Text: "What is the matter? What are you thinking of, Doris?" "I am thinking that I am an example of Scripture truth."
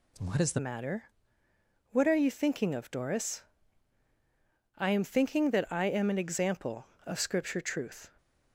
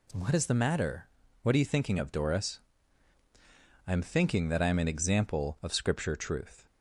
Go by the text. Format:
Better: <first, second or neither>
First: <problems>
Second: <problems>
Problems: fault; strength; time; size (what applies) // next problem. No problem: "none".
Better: second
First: changes voice at "matter"; from 0.5 s on; 7.6 s long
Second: none